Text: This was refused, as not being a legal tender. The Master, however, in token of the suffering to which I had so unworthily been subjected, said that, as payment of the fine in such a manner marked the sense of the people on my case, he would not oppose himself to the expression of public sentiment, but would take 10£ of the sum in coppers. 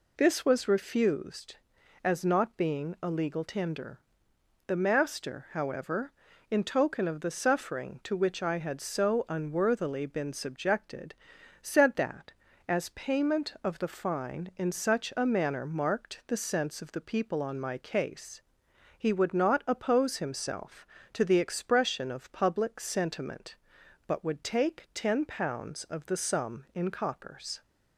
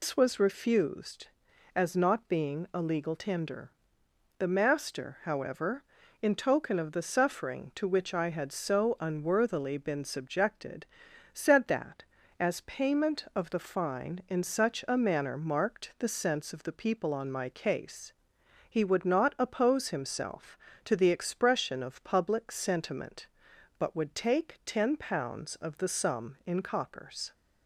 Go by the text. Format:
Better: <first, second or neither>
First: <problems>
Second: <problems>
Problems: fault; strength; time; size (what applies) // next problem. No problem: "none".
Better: first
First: none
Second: loses the start of "This"; at 0.0 s; 130 ms